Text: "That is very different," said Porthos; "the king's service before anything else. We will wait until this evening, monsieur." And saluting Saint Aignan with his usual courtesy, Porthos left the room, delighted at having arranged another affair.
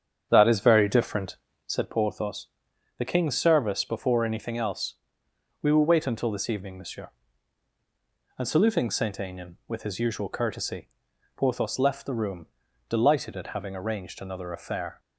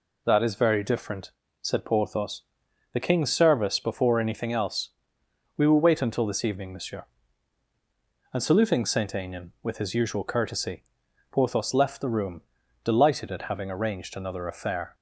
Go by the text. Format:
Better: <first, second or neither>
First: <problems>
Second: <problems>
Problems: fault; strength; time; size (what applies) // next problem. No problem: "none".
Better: second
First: starts louder than the rest; strong; until 1.8 s; 8 dB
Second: none